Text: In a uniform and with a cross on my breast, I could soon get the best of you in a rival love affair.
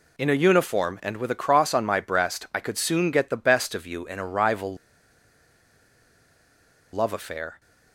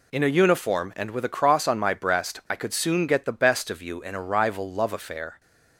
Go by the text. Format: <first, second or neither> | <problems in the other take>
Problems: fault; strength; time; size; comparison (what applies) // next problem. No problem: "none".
second | pauses between "rival" and "love"; strong; at 4.7 s; 2.1 s long